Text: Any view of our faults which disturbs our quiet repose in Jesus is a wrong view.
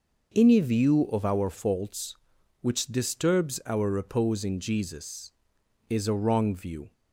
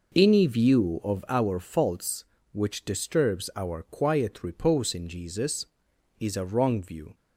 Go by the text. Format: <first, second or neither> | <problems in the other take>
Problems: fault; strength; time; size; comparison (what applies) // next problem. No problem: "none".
second | skips "quiet"; at 3.9 s